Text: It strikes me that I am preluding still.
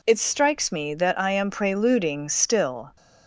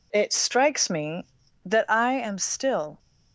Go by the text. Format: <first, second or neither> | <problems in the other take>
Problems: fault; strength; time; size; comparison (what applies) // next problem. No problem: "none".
first | skips "preluding"; at 2.4 s